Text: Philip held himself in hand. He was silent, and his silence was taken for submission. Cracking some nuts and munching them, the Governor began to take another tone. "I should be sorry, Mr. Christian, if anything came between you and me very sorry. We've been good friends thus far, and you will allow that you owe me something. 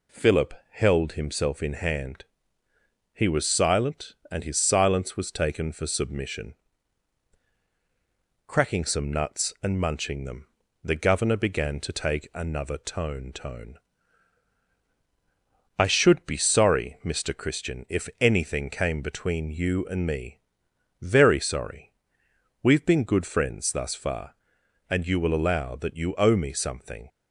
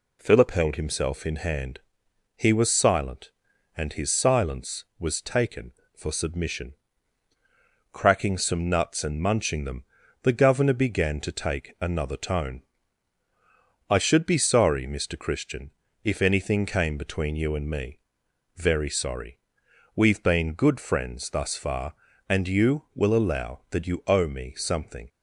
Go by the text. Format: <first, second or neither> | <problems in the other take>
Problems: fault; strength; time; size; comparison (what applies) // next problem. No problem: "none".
second | pauses between "Philip" and "held"; slight; at 0.5 s; 0.16 s long // says "tone" twice; at 13.3 s // pauses between "me" and "very"; noticeable; at 20.3 s; 0.64 s long; noticeable in the second